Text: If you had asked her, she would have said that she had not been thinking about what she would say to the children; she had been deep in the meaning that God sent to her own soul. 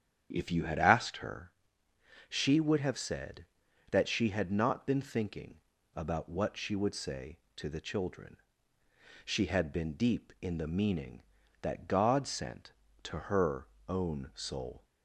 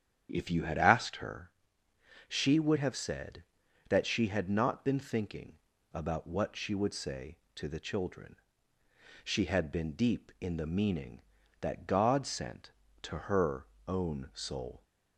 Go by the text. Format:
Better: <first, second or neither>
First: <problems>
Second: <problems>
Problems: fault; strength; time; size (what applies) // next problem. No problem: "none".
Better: neither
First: starts louder than the rest; strong; until 1.3 s; 8.5 dB // pauses between "thinking" and "about"; slight; at 5.5 s; 0.34 s long // pauses between "her" and "own"; slight; at 13.6 s; 0.22 s long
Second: starts louder than the rest; strong; until 1.3 s; 8.5 dB // pauses between "thinking" and "about"; slight; at 5.5 s; 0.34 s long // pauses between "her" and "own"; slight; at 13.6 s; 0.22 s long